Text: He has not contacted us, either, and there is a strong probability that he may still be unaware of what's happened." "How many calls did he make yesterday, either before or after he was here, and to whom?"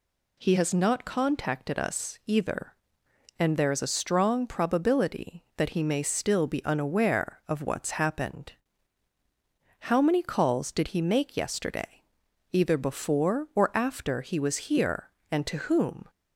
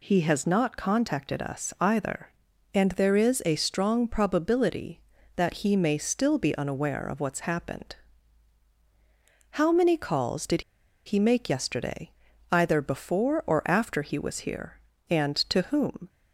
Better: first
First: none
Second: pauses between "did" and "he"; at 10.6 s; 0.43 s long

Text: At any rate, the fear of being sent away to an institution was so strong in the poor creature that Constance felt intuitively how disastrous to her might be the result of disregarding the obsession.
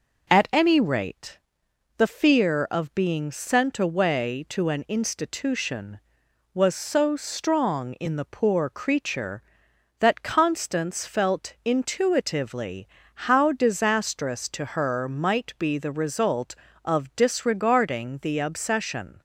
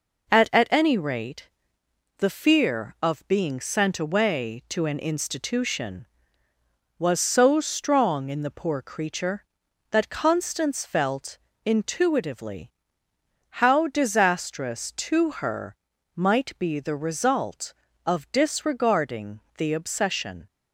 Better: first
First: pauses between "intuitively" and "how"; at 12.8 s; 0.40 s long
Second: says "At" twice; at 0.5 s // pauses between "felt" and "intuitively"; slight; at 11.3 s; 0.28 s long // pauses between "intuitively" and "how"; noticeable; at 12.7 s; 0.90 s long // pauses between "her" and "might"; at 15.7 s; 0.40 s long // pauses between "disregarding" and "the"; slight; at 19.3 s; 0.18 s long

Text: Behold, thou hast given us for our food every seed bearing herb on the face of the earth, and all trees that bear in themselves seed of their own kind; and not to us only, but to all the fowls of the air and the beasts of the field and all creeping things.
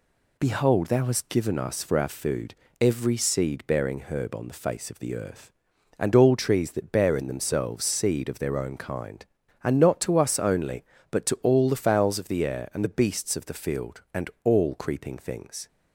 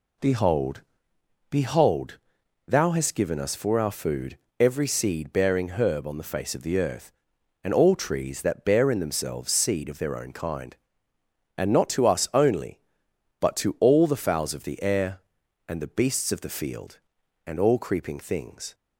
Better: first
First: pauses between "food" and "every"; slight; at 2.5 s; 0.26 s long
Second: says "Behold" twice; at 1.4 s // pauses between "food" and "every"; slight; at 4.3 s; 0.22 s long

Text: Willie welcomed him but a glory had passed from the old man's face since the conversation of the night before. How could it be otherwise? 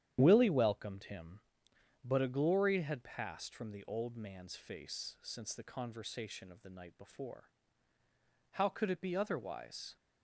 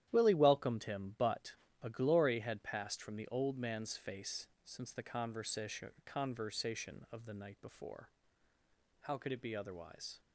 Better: first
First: starts louder than the rest; strong; until 1.2 s; 10 dB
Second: starts louder than the rest; strong; until 1.1 s; 11.5 dB // pauses between "but" and "a"; slight; at 1.5 s; 0.30 s long // pauses between "face" and "since"; slight; at 4.4 s; 0.16 s long // says "conversation" twice; at 6.0 s

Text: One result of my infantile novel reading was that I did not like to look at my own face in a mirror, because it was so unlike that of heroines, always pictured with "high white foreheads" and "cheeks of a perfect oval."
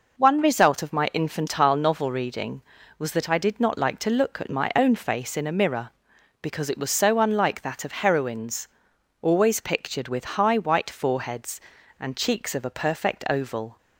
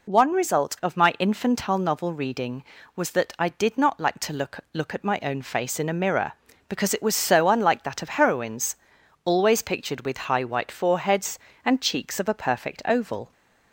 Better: first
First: none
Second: says "look" twice; at 4.7 s

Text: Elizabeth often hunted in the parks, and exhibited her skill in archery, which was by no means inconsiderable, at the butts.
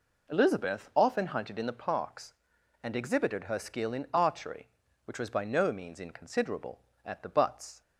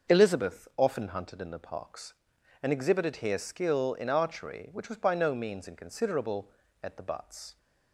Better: first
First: none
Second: says "here" for "her"; at 3.1 s

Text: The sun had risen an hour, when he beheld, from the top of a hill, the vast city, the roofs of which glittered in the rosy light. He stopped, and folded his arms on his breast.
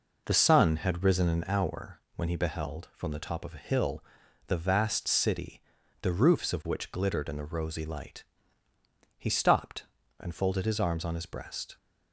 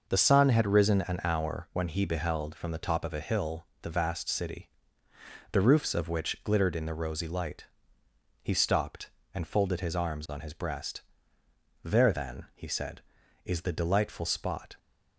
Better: first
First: none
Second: goes on to say "There then he said is the delightful spot"; strong; from 11.8 s on; 2.9 s long

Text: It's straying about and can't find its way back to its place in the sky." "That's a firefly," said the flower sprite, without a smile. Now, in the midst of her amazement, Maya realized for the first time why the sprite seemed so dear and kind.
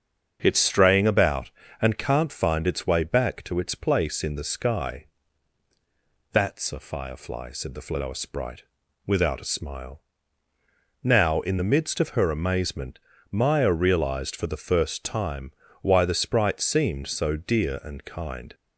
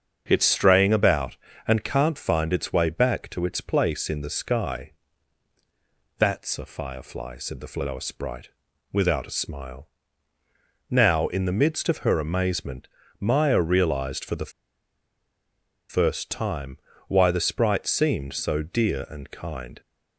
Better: first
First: starts louder than the rest; until 1.4 s; 7 dB // pauses between "time" and "why"; slight; at 15.5 s; 0.32 s long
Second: starts louder than the rest; until 1.2 s; 7 dB // pauses between "the" and "first"; strong; at 14.5 s; 1.3 s long // pauses between "time" and "why"; slight; at 16.7 s; 0.32 s long

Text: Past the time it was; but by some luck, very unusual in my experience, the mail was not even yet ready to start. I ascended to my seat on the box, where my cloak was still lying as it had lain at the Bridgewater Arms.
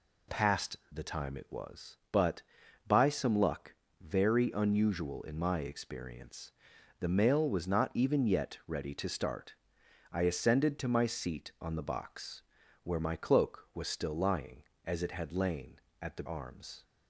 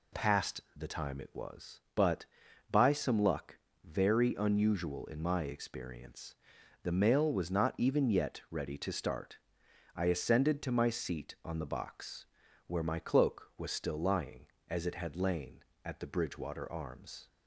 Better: second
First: skips "Bridgewater"; at 16.2 s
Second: none

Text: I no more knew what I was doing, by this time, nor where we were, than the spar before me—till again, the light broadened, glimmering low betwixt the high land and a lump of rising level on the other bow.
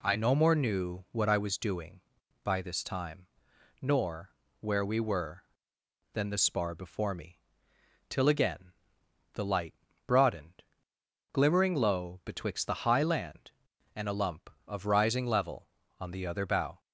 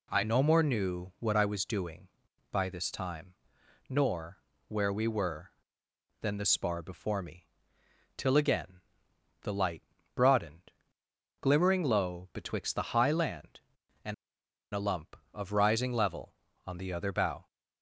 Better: first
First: pauses between "nor" and "where"; slight; at 4.3 s; 0.28 s long // pauses between "light" and "broadened"; slight; at 9.7 s; 0.32 s long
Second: pauses between "nor" and "where"; slight; at 4.3 s; 0.28 s long // pauses between "light" and "broadened"; slight; at 9.8 s; 0.32 s long // pauses between "and" and "a"; noticeable; at 14.1 s; 0.59 s long

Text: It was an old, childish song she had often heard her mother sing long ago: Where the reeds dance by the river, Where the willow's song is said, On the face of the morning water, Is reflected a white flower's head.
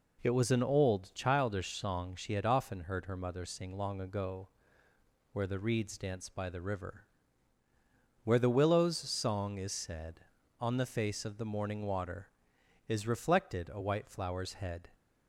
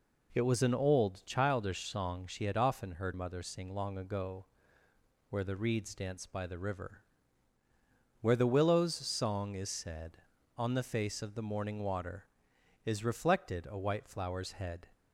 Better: first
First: none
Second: skips "her"; at 3.1 s

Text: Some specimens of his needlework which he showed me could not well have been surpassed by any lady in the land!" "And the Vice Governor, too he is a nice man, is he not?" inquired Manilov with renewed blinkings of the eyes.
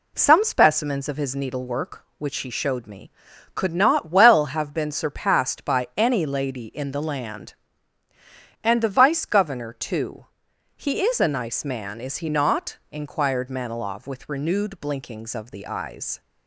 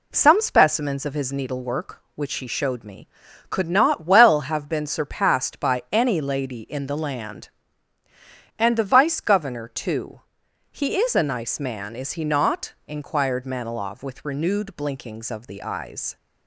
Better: neither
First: pauses between "too" and "he"; noticeable; at 10.2 s; 0.52 s long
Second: pauses between "too" and "he"; noticeable; at 10.1 s; 0.52 s long

